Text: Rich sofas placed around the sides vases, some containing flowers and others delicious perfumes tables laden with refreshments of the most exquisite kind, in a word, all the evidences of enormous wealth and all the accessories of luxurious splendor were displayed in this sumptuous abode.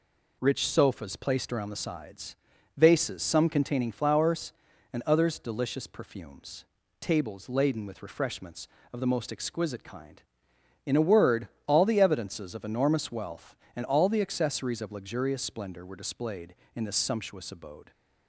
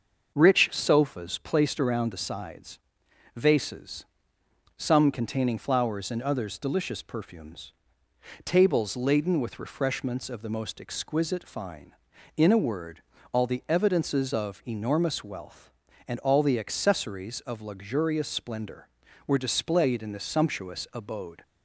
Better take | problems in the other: first | starts louder than the rest; until 1.3 s; 6.5 dB // pauses between "sides" and "vases"; noticeable; at 2.7 s; 0.56 s long; also in the first // pauses between "perfumes" and "tables"; noticeable; at 7.7 s; 0.72 s long; slight in the first // says "fine" for "kind"; at 11.4 s

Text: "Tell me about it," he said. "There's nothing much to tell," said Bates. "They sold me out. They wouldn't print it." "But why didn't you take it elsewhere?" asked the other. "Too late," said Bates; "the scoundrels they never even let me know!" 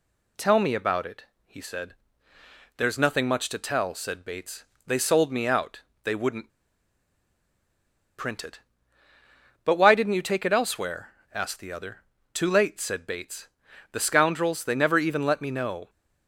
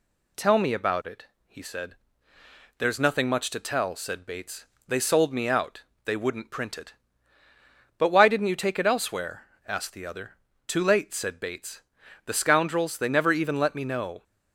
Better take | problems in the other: second | pauses between "wouldn't" and "print"; strong; at 6.4 s; 1.6 s long

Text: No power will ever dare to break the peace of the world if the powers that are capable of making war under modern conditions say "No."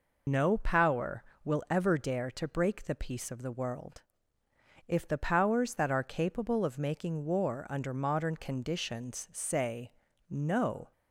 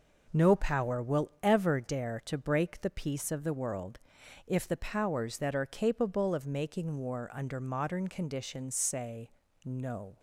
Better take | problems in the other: second | loses the start of "No"; at 0.2 s; 95 ms // pauses between "world" and "if"; noticeable; at 4.0 s; 0.86 s long; noticeable in the second // pauses between "say" and "No"; at 9.8 s; 0.40 s long; slight in the second

